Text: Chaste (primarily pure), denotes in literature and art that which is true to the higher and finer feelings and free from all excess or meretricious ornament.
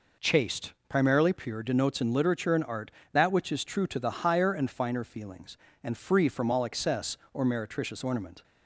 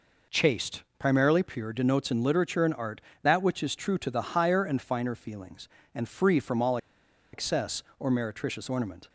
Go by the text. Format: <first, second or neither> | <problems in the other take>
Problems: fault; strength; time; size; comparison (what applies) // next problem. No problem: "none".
first | pauses between "all" and "excess"; noticeable; at 6.7 s; 0.56 s long